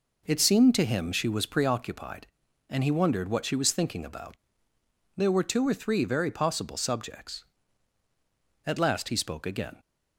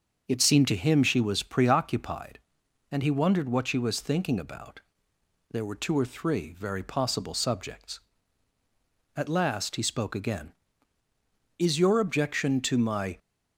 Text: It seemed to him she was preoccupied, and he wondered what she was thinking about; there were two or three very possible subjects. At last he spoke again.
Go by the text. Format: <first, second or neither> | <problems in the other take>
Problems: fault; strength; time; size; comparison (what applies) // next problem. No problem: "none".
first | starts louder than the rest; until 1.3 s; 6 dB // goes on to say "Is your objection to my"; from 11.5 s on; 1.6 s long